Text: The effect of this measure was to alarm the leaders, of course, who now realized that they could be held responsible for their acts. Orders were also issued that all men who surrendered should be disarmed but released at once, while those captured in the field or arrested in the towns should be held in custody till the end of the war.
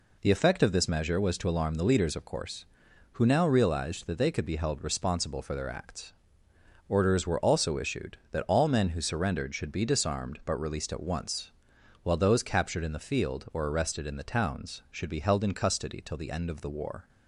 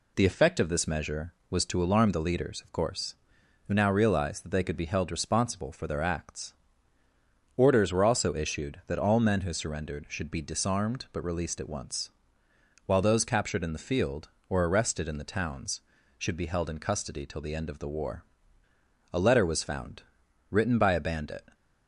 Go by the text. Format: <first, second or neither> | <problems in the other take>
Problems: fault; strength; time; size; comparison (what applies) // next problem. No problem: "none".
first | goes on to say "A letter was found written by a bandit"; strong; from 19.1 s on; 2.4 s long